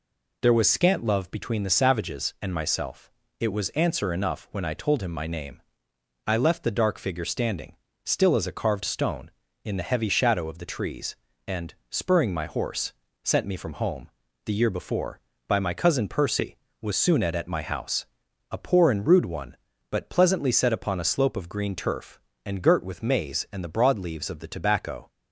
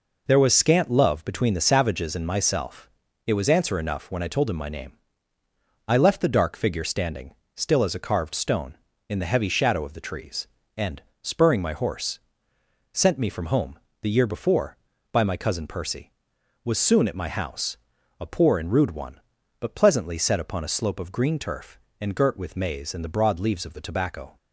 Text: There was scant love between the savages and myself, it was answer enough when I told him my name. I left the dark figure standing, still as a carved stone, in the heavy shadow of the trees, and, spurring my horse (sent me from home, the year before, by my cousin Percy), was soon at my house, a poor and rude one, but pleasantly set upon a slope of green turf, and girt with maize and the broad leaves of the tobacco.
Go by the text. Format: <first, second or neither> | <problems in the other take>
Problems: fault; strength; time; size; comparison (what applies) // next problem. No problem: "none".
second | says "at" twice; at 17.3 s